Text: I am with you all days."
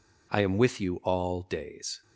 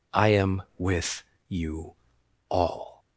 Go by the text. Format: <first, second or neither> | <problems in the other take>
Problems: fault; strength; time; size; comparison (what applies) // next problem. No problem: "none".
first | pauses between "with" and "you"; slight; at 1.2 s; 0.26 s long // pauses between "you" and "all"; noticeable; at 1.9 s; 0.56 s long // stops before "days"; at 2.9 s